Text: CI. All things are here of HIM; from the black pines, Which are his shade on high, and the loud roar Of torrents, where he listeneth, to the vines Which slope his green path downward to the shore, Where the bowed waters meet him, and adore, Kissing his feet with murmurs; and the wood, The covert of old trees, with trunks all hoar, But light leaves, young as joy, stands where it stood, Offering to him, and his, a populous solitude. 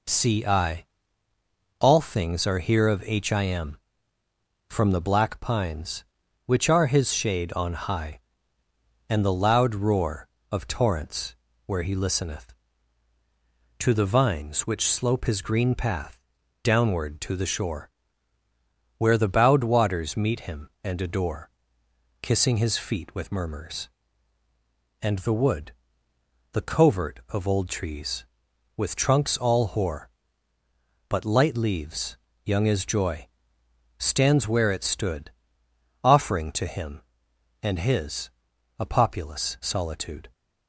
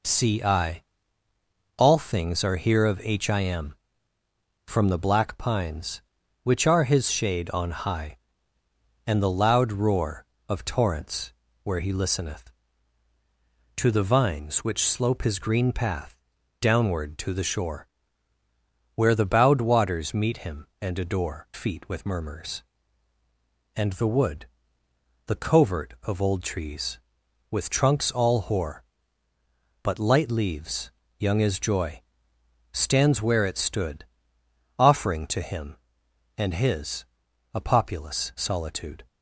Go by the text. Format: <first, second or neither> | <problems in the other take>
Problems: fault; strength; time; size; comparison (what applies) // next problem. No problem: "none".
first | pauses between "path" and "downward"; noticeable; at 16.1 s; 0.46 s long; noticeable in the first // skips "Kissing his"; at 21.4 s